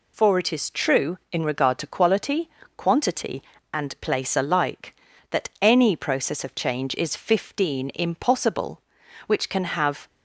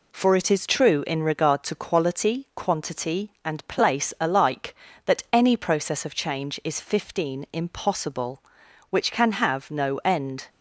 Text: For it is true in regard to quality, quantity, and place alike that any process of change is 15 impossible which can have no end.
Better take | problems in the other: second | stops before "no end"; at 10.0 s

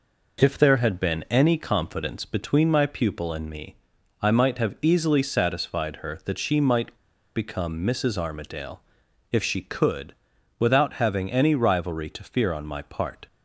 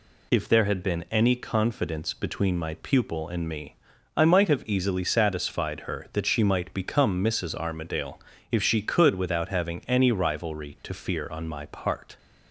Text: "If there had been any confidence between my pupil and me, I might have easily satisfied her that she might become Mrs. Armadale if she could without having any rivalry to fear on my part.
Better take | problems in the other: second | pauses between "might" and "become"; at 6.9 s; 0.39 s long // pauses between "Armadale" and "if"; noticeable; at 8.8 s; 0.48 s long; slight in the second // pauses between "could" and "without"; at 10.1 s; 0.44 s long

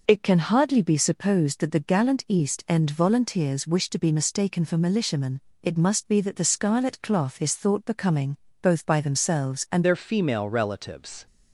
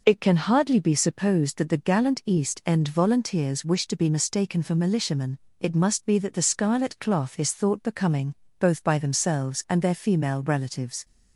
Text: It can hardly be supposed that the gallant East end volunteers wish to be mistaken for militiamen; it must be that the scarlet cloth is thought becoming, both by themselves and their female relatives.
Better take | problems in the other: second | changes voice at "their"; from 9.8 s on; 1.4 s long

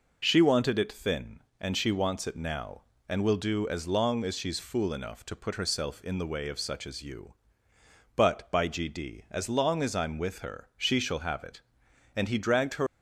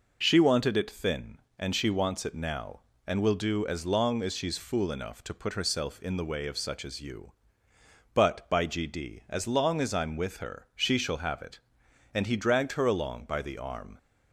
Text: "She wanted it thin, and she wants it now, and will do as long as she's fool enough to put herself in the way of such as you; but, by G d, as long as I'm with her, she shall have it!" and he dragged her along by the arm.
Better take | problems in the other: second | stops before "along by the arm"; at 12.8 s

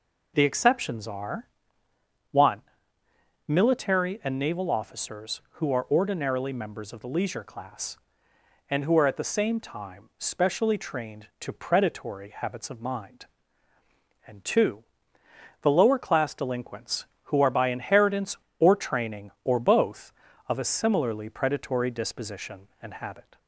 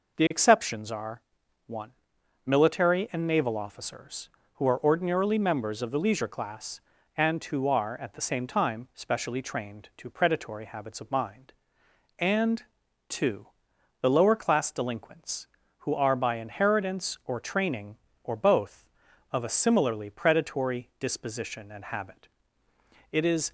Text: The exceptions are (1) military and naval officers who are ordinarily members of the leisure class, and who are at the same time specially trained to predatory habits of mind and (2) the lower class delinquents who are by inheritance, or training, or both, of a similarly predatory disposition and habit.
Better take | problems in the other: first | goes on to say "It is"; slight; from 23.1 s on; 0.40 s long

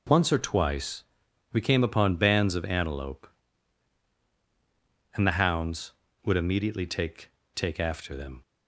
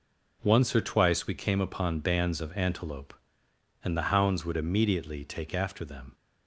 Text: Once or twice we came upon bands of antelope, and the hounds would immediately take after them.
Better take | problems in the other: second | pauses between "twice" and "we"; noticeable; at 1.0 s; 0.48 s long // says "take" twice; at 7.5 s

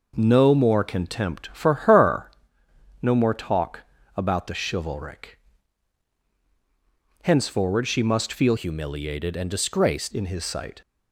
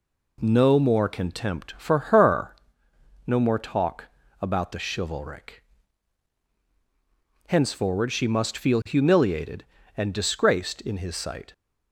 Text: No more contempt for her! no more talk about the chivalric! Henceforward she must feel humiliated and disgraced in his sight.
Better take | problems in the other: second | pauses between "talk" and "about"; slight; at 3.8 s; 0.36 s long; slight in the second // changes voice from "humiliated" to "disgraced"; from 8.5 to 10.1 s; 1.6 s long

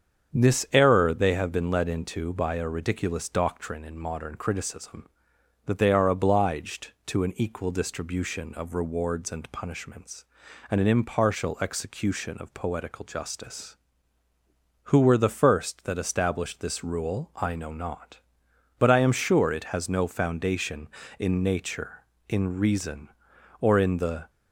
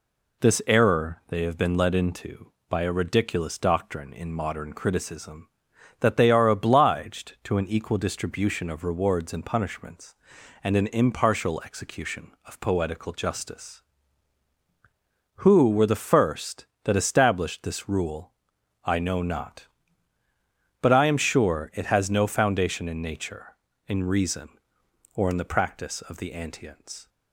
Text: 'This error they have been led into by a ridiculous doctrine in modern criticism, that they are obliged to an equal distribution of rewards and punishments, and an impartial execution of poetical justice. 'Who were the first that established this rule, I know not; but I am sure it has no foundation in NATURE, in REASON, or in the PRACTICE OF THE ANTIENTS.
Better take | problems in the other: second | starts louder than the rest; strong; until 1.4 s; 7.5 dB // stops before "PRACTICE OF THE ANTIENTS"; at 24.2 s

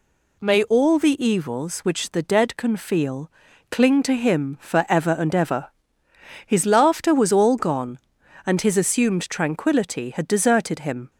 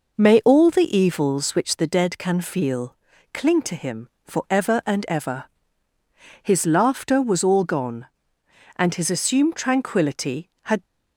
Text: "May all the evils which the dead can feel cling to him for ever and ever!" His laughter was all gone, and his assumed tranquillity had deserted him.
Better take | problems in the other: first | pauses between "feel" and "cling"; at 2.9 s; 0.38 s long; also in the first // stops before "deserted him"; at 10.8 s

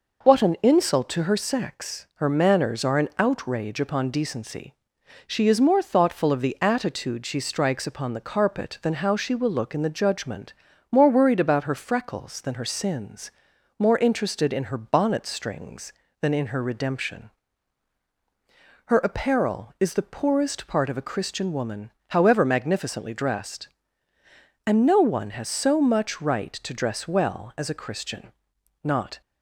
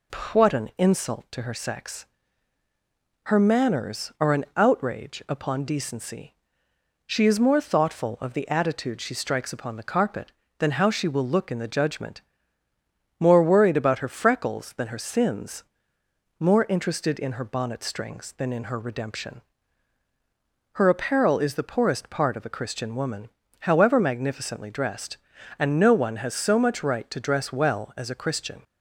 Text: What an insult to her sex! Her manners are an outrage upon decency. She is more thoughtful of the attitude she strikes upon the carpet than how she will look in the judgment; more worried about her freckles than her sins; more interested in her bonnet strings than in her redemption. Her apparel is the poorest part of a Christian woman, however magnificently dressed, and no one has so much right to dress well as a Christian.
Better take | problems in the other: second | goes on to say "Not"; slight; from 28.8 s on; 0.36 s long

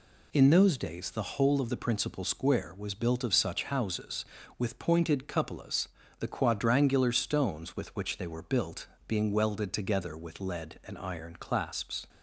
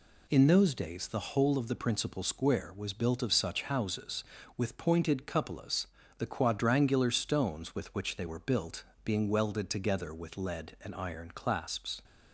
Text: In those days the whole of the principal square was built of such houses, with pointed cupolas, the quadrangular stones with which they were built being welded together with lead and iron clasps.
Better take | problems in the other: neither | pauses between "built" and "being"; slight; the same in both

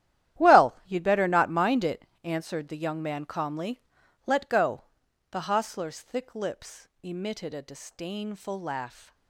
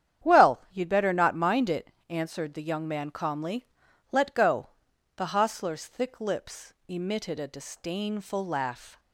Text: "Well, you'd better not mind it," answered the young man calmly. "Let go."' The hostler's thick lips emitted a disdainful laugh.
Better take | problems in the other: second | gets quieter; strong; throughout; 14.5 dB // starts louder than the rest; strong; until 1.4 s; 12 dB; strong in the second

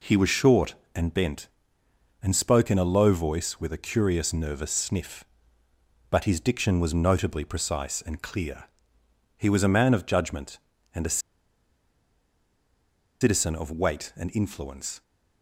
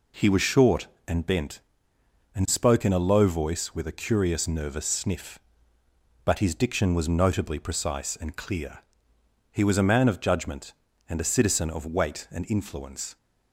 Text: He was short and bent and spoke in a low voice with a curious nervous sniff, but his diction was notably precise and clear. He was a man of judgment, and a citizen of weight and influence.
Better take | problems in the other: second | pauses between "a" and "citizen"; strong; at 11.1 s; 2.0 s long

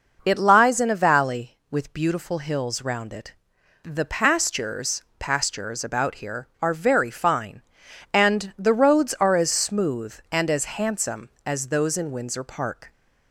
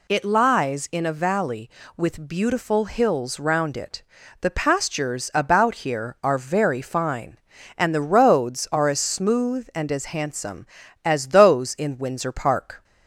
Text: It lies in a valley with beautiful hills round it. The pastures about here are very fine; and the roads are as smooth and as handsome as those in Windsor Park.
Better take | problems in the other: second | says "pastures" twice; at 5.1 s

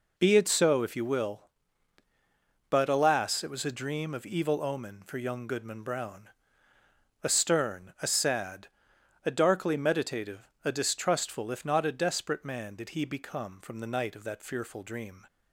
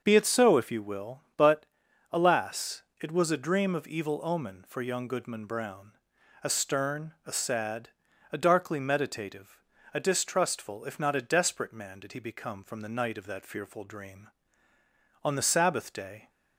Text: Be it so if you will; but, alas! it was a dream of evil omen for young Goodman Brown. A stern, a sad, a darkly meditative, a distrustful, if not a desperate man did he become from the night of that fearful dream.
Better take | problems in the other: first | starts louder than the rest; until 1.0 s; 6 dB // goes on to say "On the Sabbath day"; noticeable; from 15.2 s on; 1.0 s long

